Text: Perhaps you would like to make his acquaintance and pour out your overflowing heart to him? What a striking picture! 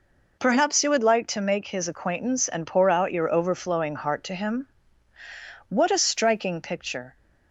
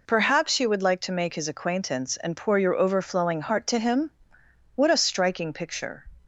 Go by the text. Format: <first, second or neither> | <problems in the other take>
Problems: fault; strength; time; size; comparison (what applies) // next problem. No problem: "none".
first | skips "out"; at 2.5 s